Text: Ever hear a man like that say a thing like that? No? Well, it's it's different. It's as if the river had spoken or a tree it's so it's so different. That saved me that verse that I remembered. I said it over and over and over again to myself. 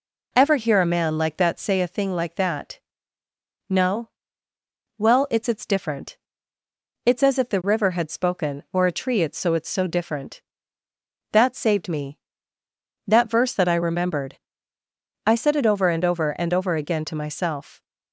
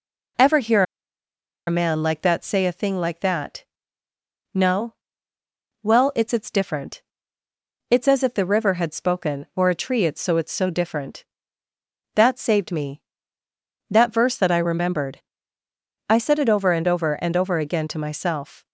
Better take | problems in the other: first | pauses between "hear" and "a"; noticeable; at 0.8 s; 0.84 s long

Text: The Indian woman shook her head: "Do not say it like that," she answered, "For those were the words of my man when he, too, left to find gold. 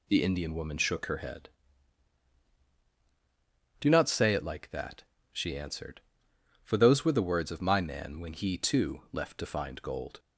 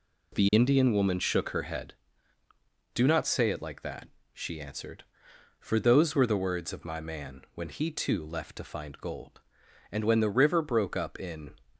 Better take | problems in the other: first | goes on to say "And when the river broke up in"; from 9.9 s on; 1.6 s long

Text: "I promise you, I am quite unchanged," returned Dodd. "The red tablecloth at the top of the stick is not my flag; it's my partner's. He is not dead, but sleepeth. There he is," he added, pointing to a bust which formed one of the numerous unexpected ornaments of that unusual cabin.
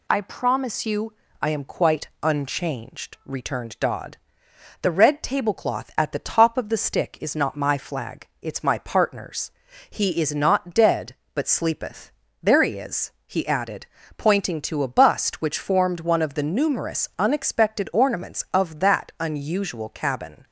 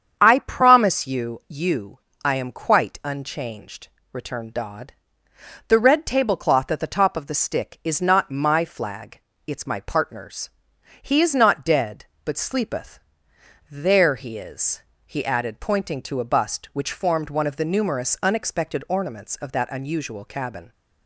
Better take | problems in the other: first | starts louder than the rest; strong; until 1.2 s; 7.5 dB // says "you" twice; at 1.4 s

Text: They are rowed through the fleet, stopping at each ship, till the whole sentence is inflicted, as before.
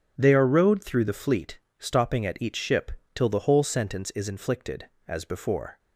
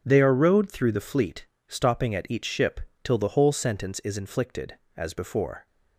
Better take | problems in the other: neither | none

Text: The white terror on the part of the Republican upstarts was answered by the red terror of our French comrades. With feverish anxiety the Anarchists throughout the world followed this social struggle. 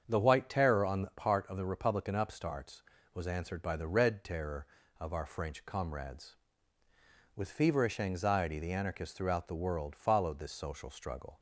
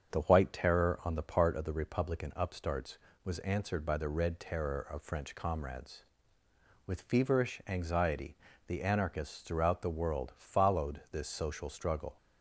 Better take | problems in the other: first | starts louder than the rest; strong; until 1.1 s; 7.5 dB; strong in the first // skips "our"; at 5.0 s // pauses between "anxiety" and "the"; slight; at 8.3 s; 0.30 s long

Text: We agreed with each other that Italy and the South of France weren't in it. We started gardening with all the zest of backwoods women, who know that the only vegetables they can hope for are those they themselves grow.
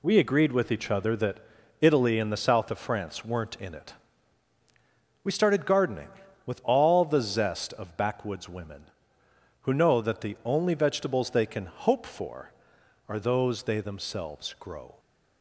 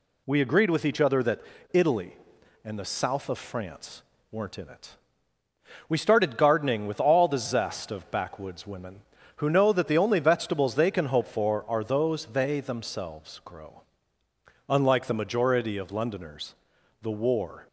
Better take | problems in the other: first | pauses between "that" and "Italy"; slight; at 1.4 s; 0.31 s long; also in the first // pauses between "France" and "weren't"; slight; at 4.0 s; 0.28 s long // goes on to say "Unlike the majority of Londoners the War"; strong; from 14.6 s on; 2.9 s long

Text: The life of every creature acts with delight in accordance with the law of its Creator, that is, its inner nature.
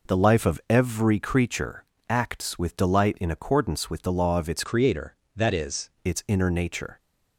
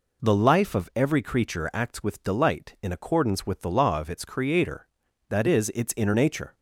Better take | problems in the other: second | pauses between "creature" and "acts"; slight; at 1.8 s; 0.26 s long // changes voice from "Creator" to "is"; from 4.6 to 5.8 s; 1.2 s long

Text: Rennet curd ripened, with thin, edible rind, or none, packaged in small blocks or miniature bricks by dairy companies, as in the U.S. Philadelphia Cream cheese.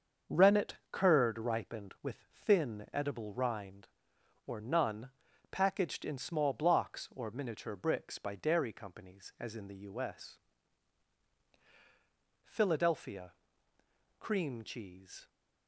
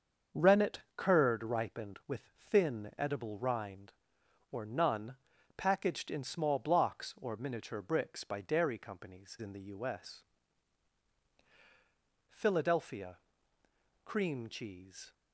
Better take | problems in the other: first | starts louder than the rest; until 1.5 s; 7 dB; also in the first // pauses between "Rennet" and "curd"; slight; at 0.7 s; 0.16 s long; slight in the first // skips "as"; at 9.3 s // pauses between "Philadelphia" and "Cream"; noticeable; at 13.1 s; 0.86 s long; noticeable in the first

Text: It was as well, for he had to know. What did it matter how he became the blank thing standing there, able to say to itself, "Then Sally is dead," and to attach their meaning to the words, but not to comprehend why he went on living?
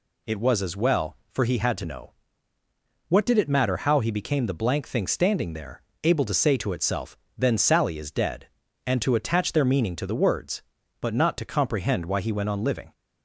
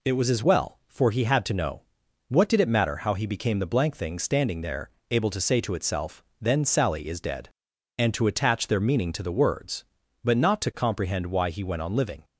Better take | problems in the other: neither | none

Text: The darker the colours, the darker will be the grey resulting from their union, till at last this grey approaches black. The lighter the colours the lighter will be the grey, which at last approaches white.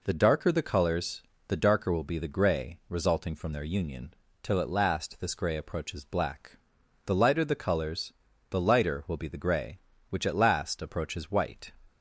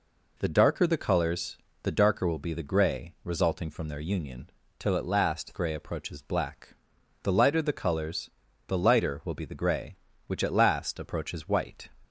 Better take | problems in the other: first | skips "this"; at 5.5 s // pauses between "colours" and "the"; at 8.2 s; 0.38 s long; also in the first

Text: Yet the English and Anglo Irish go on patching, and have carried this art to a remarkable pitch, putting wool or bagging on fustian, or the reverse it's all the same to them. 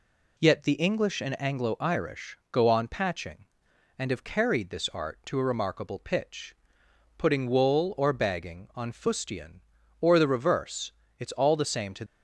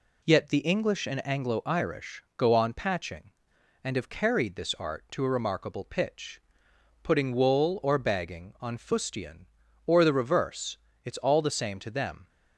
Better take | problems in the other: second | pauses between "reverse" and "it's"; slight; at 10.9 s; 0.26 s long; slight in the second // stops before "them"; at 12.0 s

